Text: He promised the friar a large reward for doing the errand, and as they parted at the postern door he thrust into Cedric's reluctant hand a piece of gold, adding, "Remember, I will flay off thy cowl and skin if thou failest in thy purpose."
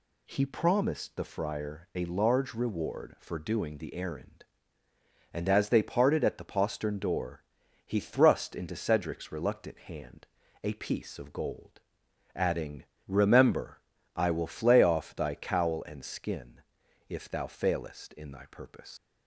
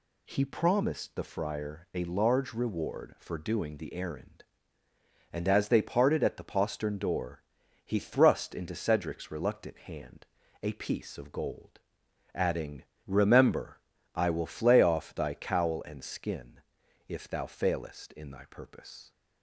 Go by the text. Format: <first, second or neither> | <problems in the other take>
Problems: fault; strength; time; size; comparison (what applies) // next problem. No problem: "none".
second | pauses between "door" and "he"; at 7.4 s; 0.42 s long; also in the second // pauses between "hand" and "a"; at 10.2 s; 0.38 s long; also in the second // pauses between "skin" and "if"; noticeable; at 16.6 s; 0.48 s long; noticeable in the second // leaves "purpose" unfinished; at 18.9 s; 150 ms